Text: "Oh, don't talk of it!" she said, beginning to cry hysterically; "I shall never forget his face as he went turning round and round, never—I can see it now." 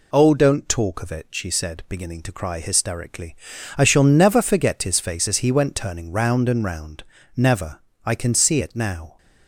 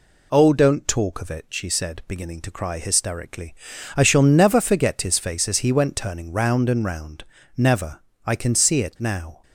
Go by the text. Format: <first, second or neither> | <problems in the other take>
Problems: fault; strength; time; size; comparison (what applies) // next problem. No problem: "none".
neither | none